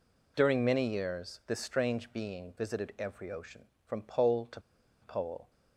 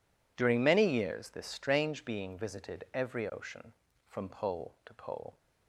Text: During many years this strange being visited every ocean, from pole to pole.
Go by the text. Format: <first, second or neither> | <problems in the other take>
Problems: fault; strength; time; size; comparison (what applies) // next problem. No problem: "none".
second | pauses between "to" and "pole"; at 4.6 s; 0.41 s long